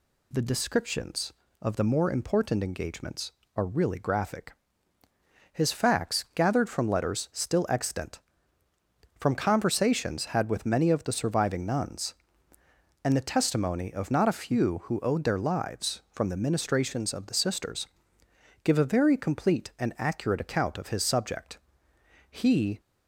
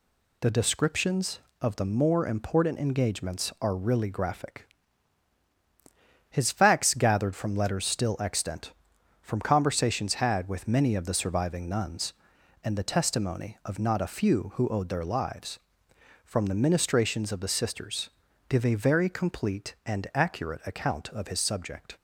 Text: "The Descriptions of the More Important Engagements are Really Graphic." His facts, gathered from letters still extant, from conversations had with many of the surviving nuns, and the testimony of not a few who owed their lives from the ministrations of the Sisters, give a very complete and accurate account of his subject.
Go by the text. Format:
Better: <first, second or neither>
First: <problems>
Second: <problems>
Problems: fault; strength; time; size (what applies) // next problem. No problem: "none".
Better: second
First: goes on to say "He"; from 22.2 s on; 0.50 s long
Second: none